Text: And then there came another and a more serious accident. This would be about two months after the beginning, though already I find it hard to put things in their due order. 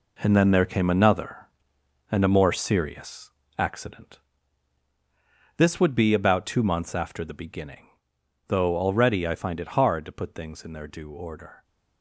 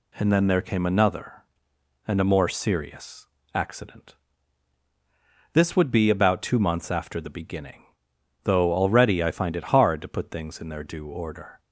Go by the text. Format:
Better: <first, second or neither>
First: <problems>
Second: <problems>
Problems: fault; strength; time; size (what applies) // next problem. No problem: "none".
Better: second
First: gets quieter; strong; throughout; 9.5 dB // pauses between "serious" and "accident"; slight; at 3.3 s; 0.26 s long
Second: pauses between "serious" and "accident"; slight; at 3.2 s; 0.26 s long